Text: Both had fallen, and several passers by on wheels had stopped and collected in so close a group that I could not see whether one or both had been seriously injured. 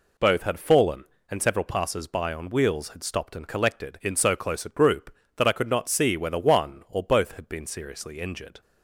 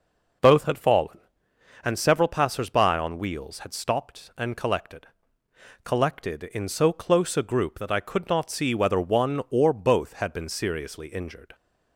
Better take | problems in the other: first | says "collected" twice; at 5.8 s

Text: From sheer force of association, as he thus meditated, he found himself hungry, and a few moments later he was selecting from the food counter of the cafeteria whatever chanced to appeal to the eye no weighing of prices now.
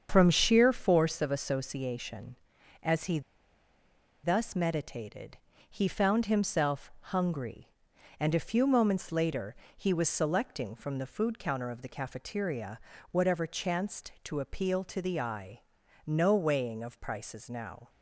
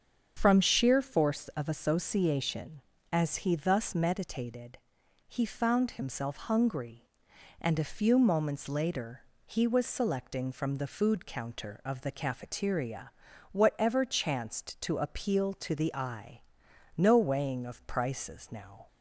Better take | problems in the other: second | starts louder than the rest; strong; until 1.1 s; 7.5 dB; strong in the second // pauses between "he" and "thus"; at 3.2 s; 1.0 s long // pauses between "later" and "he"; slight; at 9.5 s; 0.22 s long; slight in the second // pauses between "cafeteria" and "whatever"; slight; at 12.7 s; 0.32 s long; also in the second // pauses between "eye" and "no"; noticeable; at 15.5 s; 0.48 s long; noticeable in the second

